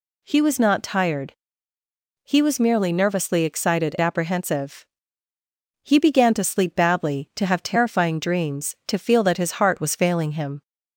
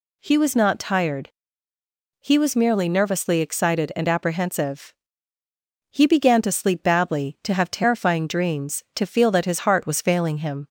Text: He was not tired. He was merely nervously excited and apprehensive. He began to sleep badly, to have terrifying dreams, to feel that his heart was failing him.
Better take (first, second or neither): second